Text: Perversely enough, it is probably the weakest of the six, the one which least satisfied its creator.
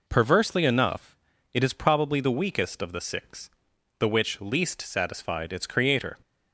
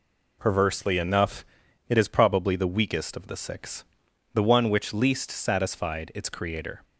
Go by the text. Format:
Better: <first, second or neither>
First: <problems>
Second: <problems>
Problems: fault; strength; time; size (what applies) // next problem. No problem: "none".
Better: second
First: skips "one"; at 4.0 s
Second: none